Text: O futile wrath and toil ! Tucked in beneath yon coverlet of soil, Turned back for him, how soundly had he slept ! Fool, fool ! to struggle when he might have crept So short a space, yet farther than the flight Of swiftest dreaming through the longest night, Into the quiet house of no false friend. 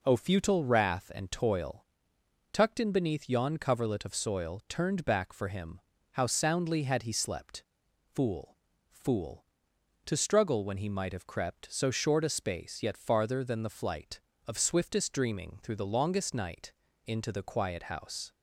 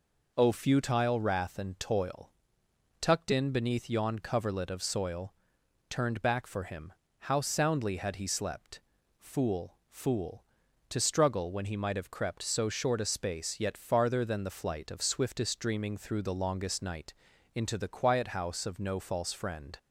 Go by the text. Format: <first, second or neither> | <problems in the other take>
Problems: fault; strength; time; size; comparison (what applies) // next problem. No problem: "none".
second | stops before "of no false friend"; at 18.3 s